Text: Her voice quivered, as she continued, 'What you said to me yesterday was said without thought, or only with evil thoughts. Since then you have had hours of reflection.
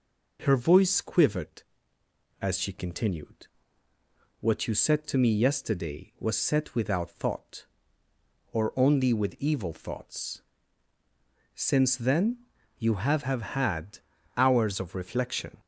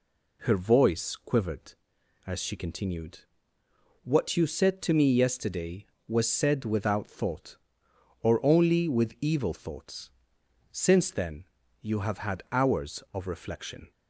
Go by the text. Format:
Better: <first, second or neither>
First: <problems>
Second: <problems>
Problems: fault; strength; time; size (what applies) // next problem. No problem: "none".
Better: second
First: pauses between "then" and "you"; at 12.3 s; 0.40 s long // says "have" twice; at 13.2 s // pauses between "had" and "hours"; slight; at 13.9 s; 0.36 s long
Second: pauses between "then" and "you"; at 11.4 s; 0.38 s long